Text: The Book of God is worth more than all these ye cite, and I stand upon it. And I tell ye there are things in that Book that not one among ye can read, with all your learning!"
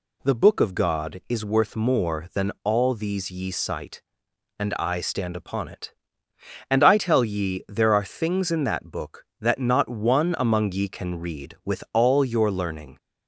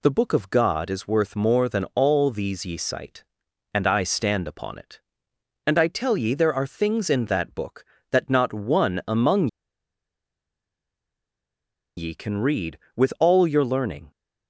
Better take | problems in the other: first | pauses between "among" and "ye"; strong; at 9.4 s; 2.5 s long

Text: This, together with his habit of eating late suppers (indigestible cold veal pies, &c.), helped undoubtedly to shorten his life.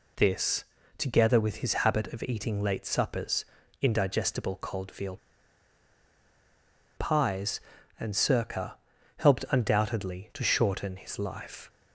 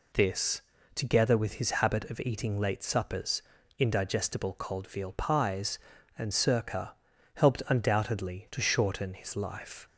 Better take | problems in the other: second | pauses between "veal" and "pies"; strong; at 5.1 s; 1.7 s long

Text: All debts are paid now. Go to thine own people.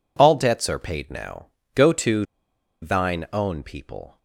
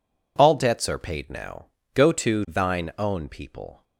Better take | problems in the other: second | pauses between "to" and "thine"; noticeable; at 2.2 s; 0.56 s long

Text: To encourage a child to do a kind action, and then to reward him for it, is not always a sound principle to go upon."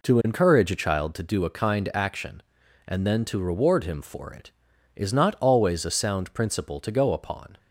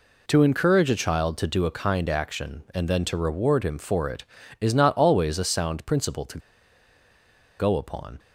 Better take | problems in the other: first | pauses between "to" and "go"; at 6.3 s; 1.2 s long

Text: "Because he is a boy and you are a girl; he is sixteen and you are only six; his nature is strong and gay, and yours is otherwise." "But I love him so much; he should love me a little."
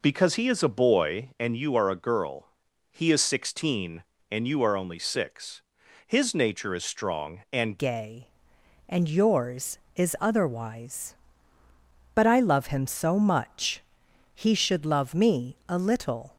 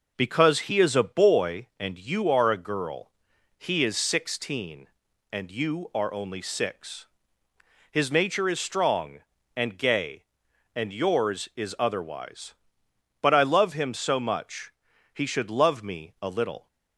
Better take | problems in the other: second | changes voice at "gay"; from 7.7 s on; 8.6 s long

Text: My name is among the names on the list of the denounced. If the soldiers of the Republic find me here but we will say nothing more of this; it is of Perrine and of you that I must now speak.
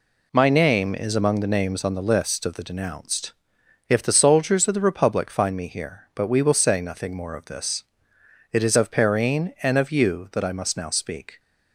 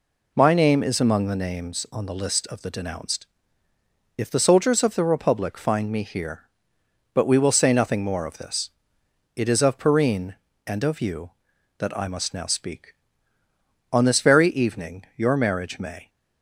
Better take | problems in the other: first | goes on to say "On this very evening your marriage may"; strong; from 13.9 s on; 2.1 s long

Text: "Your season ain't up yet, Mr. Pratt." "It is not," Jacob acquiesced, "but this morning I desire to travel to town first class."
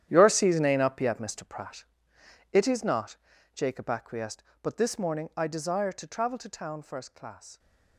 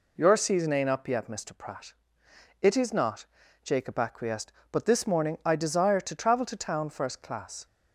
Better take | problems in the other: second | gets quieter; strong; throughout; 14 dB

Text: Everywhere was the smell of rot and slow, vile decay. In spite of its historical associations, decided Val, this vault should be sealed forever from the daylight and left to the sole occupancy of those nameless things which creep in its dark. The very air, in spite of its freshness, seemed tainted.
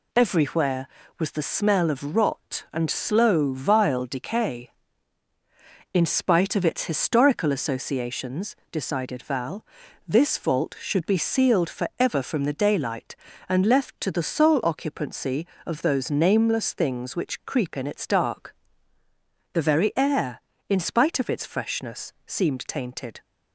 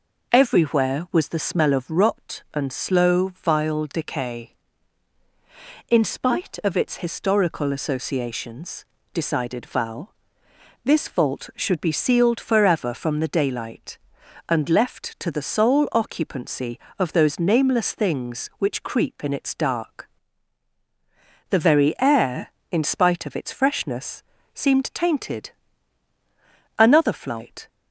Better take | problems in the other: first | goes on to say "Another flight"; noticeable; from 26.7 s on; 0.90 s long

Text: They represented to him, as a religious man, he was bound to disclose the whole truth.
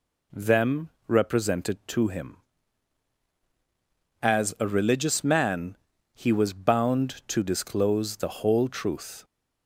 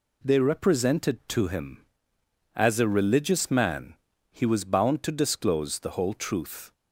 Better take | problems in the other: second | says "Them" for "They"; at 0.3 s

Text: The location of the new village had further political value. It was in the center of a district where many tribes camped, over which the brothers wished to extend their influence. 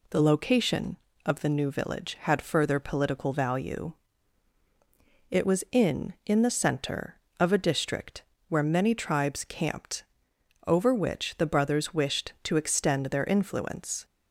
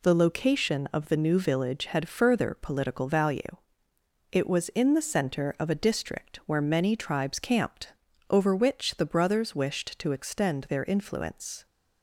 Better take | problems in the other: second | says "in" twice; at 6.2 s // pauses between "district" and "where"; slight; at 8.2 s; 0.26 s long

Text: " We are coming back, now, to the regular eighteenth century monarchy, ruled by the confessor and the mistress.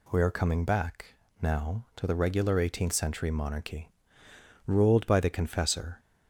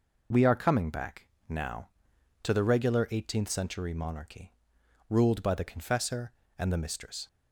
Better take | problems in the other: second | stops before "and the mistress"; at 5.9 s

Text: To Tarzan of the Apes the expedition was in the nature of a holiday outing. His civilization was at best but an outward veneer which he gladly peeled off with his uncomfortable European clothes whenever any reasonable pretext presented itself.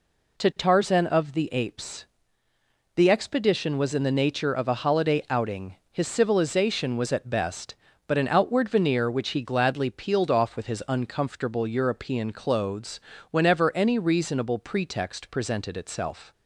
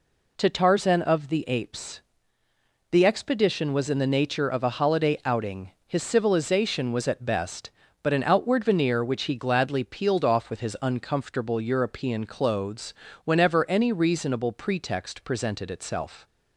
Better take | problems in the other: neither | pauses between "Apes" and "the"; noticeable; the same in both // pauses between "clothes" and "whenever"; slight; the same in both

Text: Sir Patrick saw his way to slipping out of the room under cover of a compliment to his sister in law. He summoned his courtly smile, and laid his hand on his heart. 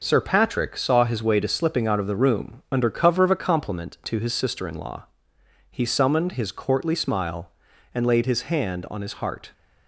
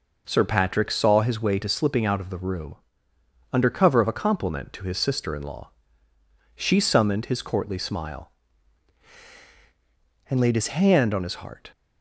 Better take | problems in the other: first | pauses between "room" and "under"; noticeable; at 2.7 s; 0.78 s long // says "She" for "He"; at 6.5 s

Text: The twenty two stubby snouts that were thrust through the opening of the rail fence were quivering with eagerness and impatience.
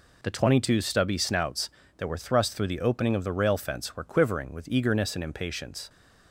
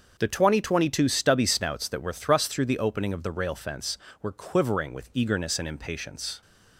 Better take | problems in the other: first | starts louder than the rest; until 1.1 s; 6.5 dB // says "twenty" twice; at 0.6 s

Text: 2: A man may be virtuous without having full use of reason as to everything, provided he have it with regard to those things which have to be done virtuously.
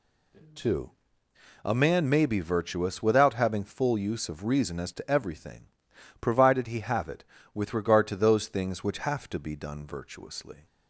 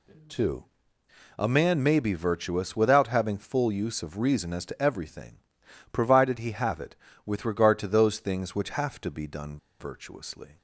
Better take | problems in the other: first | pauses between "done" and "virtuously"; slight; at 9.5 s; 0.23 s long

